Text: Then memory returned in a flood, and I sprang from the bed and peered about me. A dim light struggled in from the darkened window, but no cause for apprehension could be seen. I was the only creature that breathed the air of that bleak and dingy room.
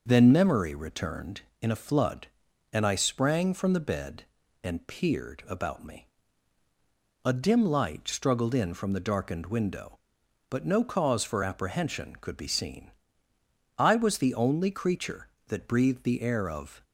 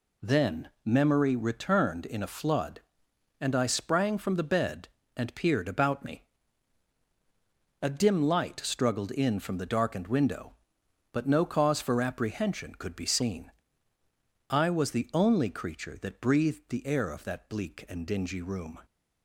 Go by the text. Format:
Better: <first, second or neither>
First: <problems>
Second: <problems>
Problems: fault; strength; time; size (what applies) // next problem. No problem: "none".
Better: second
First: stops before "that bleak and dingy room"; at 16.8 s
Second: none